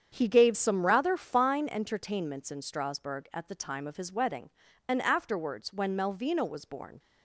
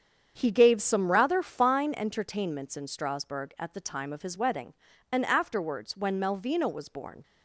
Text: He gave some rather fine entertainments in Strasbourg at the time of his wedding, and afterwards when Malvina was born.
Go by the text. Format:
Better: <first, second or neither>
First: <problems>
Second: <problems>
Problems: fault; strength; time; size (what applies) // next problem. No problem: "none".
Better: neither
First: starts louder than the rest; strong; until 1.1 s; 8 dB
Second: starts louder than the rest; strong; until 1.3 s; 7.5 dB